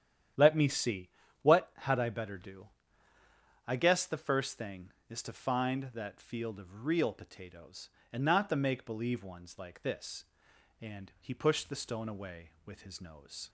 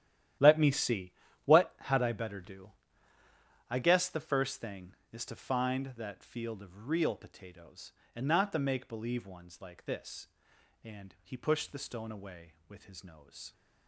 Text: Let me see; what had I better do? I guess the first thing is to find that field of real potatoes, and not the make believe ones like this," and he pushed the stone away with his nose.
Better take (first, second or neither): first